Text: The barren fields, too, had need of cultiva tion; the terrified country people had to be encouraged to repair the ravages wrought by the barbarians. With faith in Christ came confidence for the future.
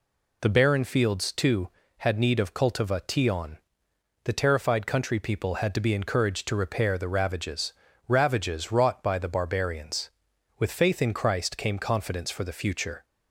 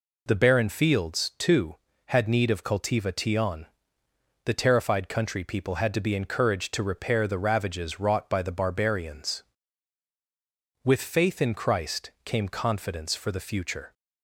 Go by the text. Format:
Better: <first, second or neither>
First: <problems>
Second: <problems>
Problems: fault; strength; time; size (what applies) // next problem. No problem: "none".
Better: second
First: says "ravages" twice; at 8.0 s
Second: none